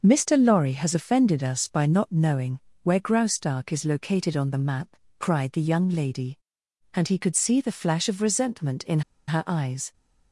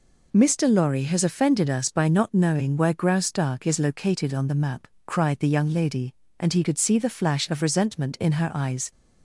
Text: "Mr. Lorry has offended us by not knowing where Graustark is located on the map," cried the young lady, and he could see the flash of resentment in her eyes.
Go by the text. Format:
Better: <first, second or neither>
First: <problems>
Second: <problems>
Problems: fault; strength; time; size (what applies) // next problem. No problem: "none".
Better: second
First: starts louder than the rest; noticeable; until 1.0 s; 6 dB // pauses between "knowing" and "where"; slight; at 2.6 s; 0.22 s long // pauses between "in" and "her"; slight; at 9.0 s; 0.27 s long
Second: none